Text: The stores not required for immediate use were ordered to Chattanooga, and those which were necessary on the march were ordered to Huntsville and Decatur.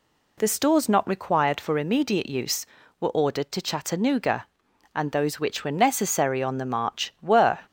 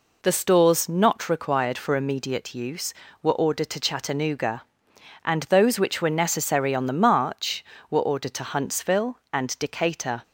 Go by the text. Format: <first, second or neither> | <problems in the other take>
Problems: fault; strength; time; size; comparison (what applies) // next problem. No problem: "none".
second | stops before "ordered to Huntsville and Decatur"; at 7.6 s